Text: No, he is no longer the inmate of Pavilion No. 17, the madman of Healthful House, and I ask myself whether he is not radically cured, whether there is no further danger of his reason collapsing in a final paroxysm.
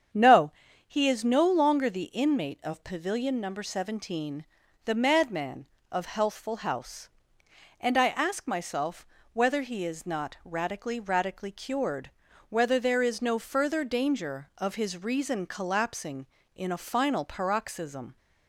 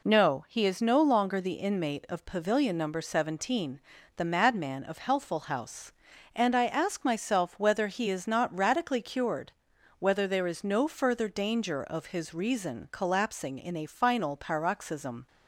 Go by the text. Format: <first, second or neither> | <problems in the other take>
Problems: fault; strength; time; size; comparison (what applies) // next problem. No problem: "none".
second | starts louder than the rest; strong; until 1.4 s; 8 dB // pauses between "myself" and "whether"; slight; at 9.0 s; 0.28 s long // says "radically" twice; at 10.9 s